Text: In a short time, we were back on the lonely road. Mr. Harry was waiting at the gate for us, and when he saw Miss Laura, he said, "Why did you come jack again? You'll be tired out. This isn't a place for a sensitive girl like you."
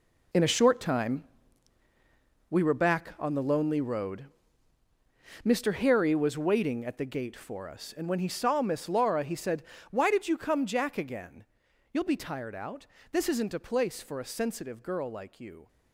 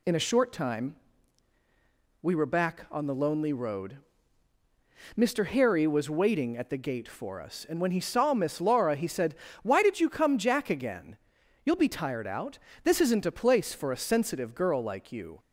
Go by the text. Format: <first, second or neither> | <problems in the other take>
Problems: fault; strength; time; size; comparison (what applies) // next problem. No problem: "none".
second | gets quieter; strong; throughout; 12 dB